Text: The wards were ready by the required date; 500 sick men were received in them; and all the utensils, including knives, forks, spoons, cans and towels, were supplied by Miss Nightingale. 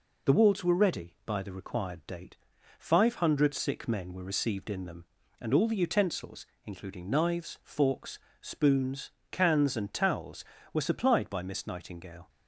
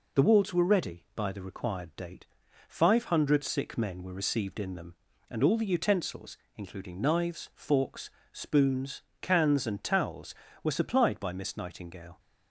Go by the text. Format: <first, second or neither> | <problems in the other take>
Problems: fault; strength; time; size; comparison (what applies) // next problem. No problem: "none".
neither | none